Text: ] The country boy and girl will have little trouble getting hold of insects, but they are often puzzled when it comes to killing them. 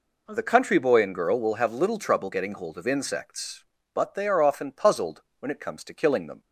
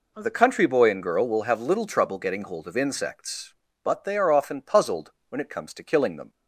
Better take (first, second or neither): neither